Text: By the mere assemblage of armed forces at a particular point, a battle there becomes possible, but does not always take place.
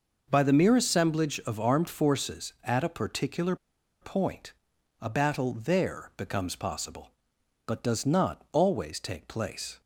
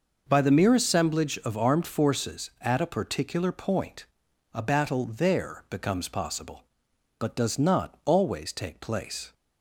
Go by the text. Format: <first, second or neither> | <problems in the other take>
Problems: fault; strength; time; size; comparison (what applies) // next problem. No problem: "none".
second | pauses between "particular" and "point"; noticeable; at 3.5 s; 0.46 s long